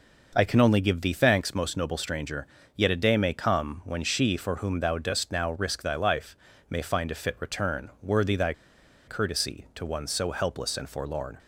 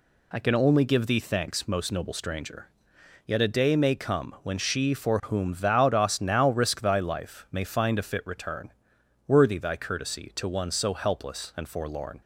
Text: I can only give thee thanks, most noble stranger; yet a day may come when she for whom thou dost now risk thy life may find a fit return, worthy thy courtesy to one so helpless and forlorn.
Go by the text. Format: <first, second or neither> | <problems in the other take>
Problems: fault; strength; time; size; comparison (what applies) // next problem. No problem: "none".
second | pauses between "life" and "may"; slight; at 6.3 s; 0.32 s long // pauses between "thy" and "courtesy"; noticeable; at 8.5 s; 0.55 s long